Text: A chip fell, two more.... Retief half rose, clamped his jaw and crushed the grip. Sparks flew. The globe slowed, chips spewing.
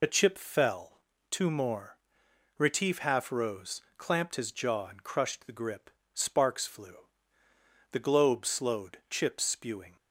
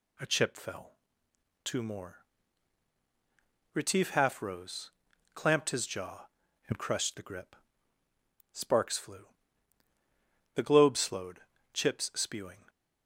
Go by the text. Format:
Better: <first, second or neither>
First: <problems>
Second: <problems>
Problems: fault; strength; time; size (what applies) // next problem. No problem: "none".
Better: second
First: loses the start of "A"; at 0.0 s; 40 ms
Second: none